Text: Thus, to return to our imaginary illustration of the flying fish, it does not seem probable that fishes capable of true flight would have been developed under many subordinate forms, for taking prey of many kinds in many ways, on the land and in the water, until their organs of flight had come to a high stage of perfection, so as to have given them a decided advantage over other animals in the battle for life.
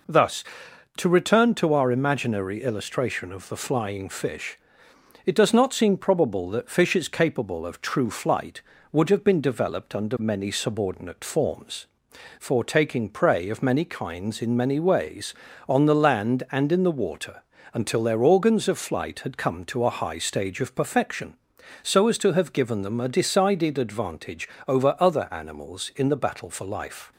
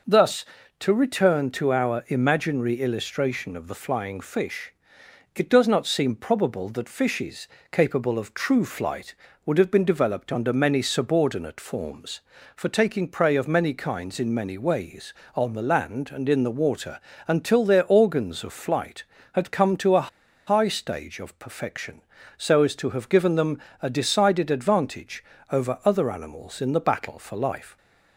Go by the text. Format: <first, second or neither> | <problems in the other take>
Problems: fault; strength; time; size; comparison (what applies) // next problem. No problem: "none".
first | pauses between "fishes" and "capable"; slight; at 7.4 s; 0.24 s long // pauses between "a" and "high"; at 20.0 s; 0.39 s long // pauses between "them" and "a"; slight; at 23.5 s; 0.24 s long // pauses between "advantage" and "over"; slight; at 25.2 s; 0.30 s long; slight in the first